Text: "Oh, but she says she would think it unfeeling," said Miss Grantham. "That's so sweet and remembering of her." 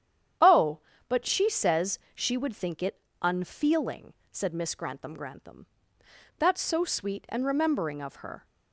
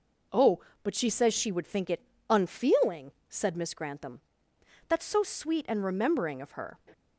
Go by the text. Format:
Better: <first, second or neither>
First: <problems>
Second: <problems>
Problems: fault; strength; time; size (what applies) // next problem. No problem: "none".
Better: second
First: starts louder than the rest; strong; until 1.7 s; 9.5 dB // pauses between "it" and "unfeeling"; slight; at 2.9 s; 0.22 s long // says "Grantham" twice; at 5.1 s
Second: pauses between "it" and "unfeeling"; slight; at 2.0 s; 0.26 s long